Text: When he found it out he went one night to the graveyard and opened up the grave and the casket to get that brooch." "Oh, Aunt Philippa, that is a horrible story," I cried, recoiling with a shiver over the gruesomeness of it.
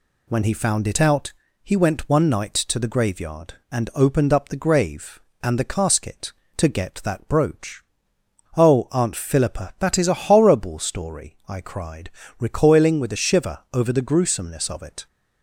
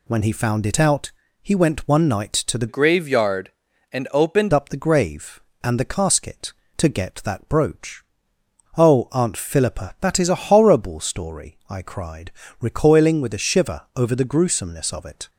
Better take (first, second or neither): first